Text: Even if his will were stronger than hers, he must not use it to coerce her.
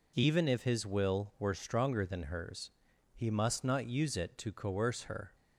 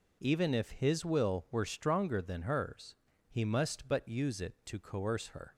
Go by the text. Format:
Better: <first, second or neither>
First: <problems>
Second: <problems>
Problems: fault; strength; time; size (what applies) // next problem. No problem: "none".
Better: first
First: none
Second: says "but" for "not"; at 3.8 s